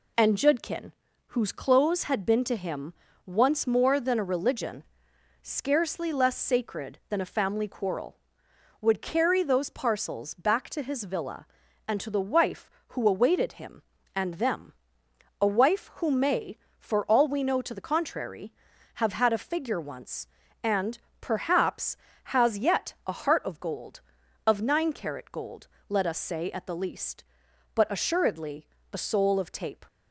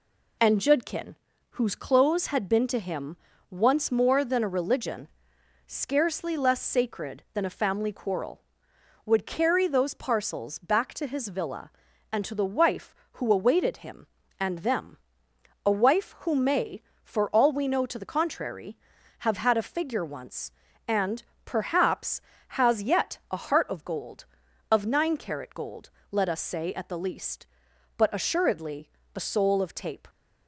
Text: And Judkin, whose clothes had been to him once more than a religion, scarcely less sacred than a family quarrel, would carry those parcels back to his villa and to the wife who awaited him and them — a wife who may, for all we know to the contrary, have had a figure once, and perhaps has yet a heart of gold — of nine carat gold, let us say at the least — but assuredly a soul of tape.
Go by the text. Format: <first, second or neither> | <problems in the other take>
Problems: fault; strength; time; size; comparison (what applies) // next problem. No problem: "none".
neither | pauses between "him" and "once"; slight; the same in both // pauses between "and" and "perhaps"; slight; the same in both // pauses between "assuredly" and "a"; slight; the same in both